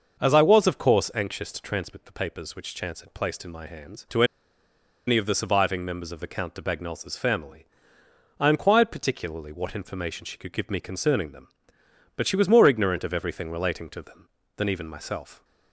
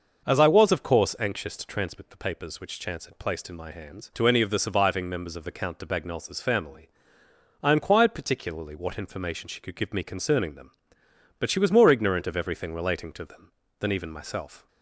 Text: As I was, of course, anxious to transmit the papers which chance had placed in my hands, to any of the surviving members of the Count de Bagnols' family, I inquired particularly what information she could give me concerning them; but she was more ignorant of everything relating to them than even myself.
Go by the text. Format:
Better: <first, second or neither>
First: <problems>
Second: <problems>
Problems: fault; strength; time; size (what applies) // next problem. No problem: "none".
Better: second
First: starts louder than the rest; noticeable; until 1.2 s; 6 dB // pauses between "to" and "any"; noticeable; at 4.2 s; 0.83 s long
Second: none